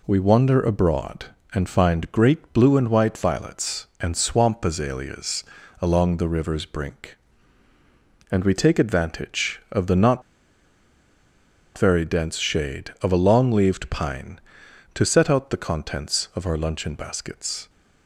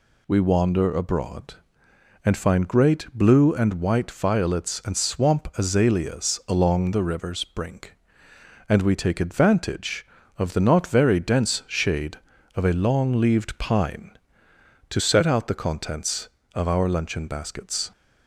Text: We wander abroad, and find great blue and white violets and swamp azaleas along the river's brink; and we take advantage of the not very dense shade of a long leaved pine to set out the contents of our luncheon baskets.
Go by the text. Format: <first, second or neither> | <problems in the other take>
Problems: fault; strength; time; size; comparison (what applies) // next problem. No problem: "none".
second | pauses between "azaleas" and "along"; slight; at 5.4 s; 0.36 s long // pauses between "not" and "very"; strong; at 10.2 s; 1.5 s long